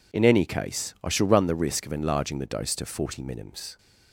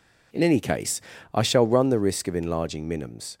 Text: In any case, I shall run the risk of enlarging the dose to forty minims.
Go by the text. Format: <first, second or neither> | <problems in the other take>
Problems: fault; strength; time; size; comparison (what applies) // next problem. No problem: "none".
first | skips "the dose to forty"; at 2.8 s